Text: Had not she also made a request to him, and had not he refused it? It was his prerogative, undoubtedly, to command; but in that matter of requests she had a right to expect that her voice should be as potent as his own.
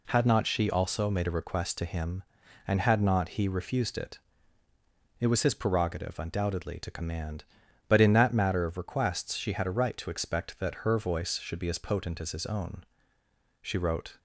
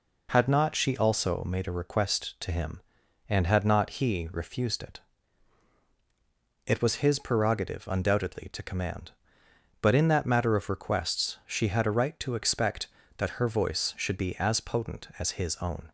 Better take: second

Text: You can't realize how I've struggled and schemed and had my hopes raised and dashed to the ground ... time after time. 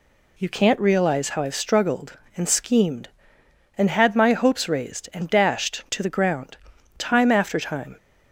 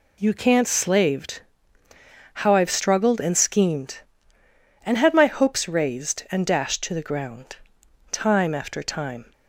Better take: first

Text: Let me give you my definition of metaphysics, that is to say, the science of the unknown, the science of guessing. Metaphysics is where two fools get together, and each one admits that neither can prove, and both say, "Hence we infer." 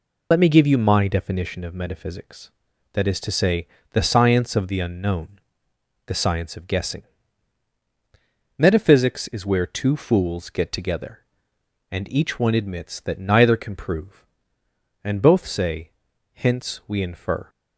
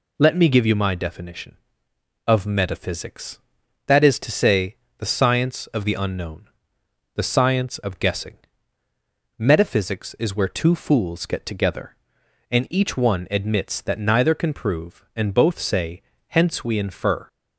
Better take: second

